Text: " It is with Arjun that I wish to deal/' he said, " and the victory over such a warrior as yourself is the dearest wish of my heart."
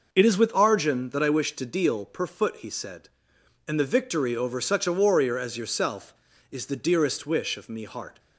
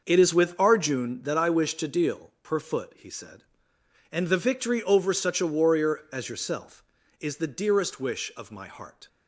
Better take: second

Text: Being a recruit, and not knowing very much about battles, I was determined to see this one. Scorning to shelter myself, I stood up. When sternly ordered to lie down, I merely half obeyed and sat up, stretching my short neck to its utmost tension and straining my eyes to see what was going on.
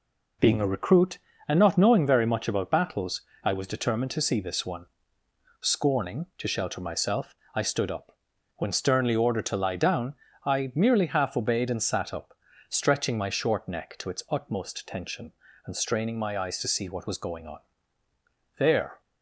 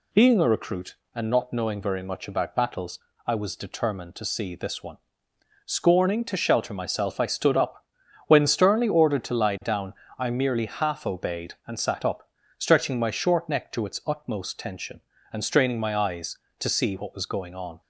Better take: second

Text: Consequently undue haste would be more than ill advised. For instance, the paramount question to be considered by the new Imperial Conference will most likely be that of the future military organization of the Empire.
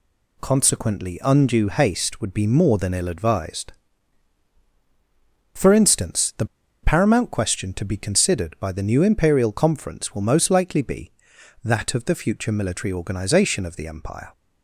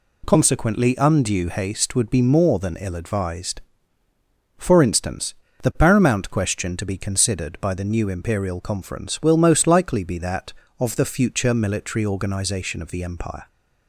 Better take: second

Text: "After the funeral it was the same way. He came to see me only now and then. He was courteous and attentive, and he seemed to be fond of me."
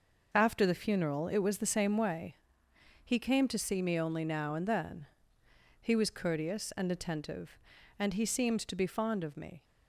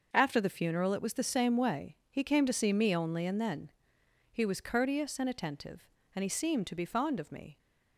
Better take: first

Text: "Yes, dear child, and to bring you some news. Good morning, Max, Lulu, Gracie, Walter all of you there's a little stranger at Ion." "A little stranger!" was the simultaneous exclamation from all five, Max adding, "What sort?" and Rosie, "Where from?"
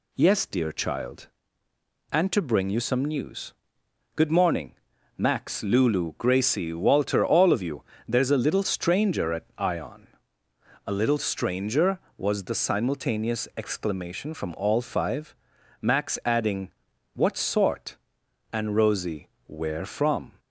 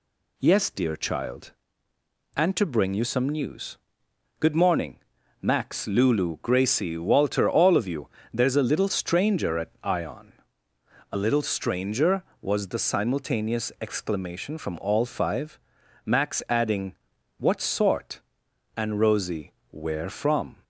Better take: neither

